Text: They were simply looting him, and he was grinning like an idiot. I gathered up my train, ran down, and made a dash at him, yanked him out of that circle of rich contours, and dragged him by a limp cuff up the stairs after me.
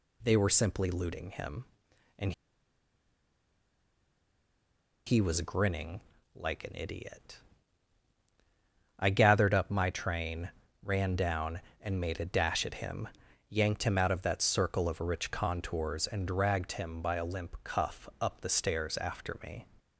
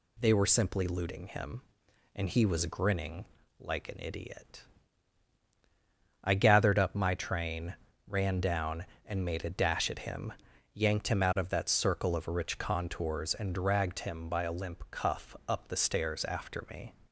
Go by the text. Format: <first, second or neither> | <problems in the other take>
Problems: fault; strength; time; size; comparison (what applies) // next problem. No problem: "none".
second | pauses between "and" and "he"; strong; at 2.3 s; 2.7 s long // pauses between "grinning" and "like"; slight; at 6.0 s; 0.34 s long; slight in the second